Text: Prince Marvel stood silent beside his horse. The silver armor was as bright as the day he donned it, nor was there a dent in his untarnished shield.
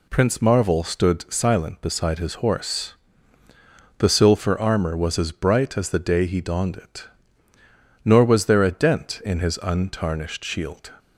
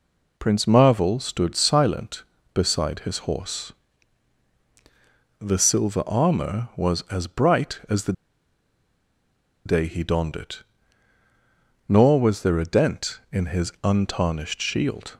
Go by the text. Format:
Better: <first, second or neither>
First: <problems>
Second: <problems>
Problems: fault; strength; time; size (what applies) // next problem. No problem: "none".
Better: first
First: none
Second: pauses between "the" and "day"; strong; at 8.1 s; 1.5 s long